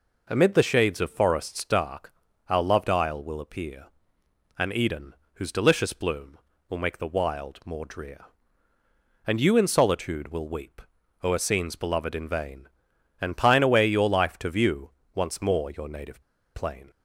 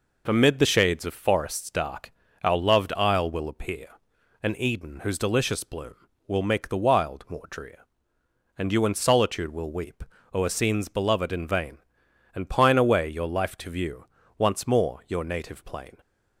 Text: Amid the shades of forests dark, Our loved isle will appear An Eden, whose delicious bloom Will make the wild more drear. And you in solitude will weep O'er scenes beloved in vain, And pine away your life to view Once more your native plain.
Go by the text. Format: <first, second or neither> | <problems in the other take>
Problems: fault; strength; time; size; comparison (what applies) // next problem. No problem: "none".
second | pauses between "appear" and "An"; noticeable; at 3.8 s; 0.72 s long; noticeable in the second // pauses between "weep" and "O'er"; at 10.8 s; 0.42 s long; slight in the second // pauses between "view" and "Once"; slight; at 14.8 s; 0.26 s long; slight in the second // pauses between "native" and "plain"; slight; at 16.2 s; 0.33 s long